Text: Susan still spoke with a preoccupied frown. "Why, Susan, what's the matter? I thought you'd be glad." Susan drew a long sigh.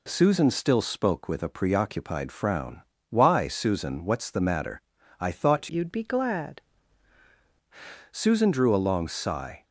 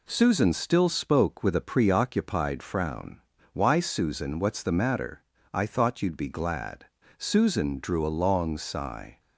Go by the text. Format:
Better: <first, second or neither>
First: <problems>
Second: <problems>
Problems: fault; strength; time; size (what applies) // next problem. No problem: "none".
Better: second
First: changes voice from "you'd" to "glad"; from 5.7 to 6.6 s; 0.9 s long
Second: none